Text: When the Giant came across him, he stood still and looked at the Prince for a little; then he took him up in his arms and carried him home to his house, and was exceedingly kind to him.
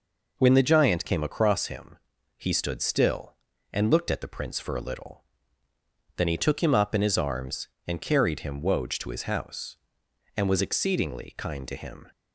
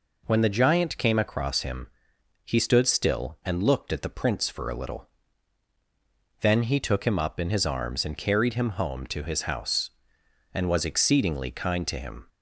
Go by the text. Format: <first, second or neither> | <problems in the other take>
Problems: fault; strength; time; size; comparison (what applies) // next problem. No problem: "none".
second | says "woj" for "home"; at 8.5 s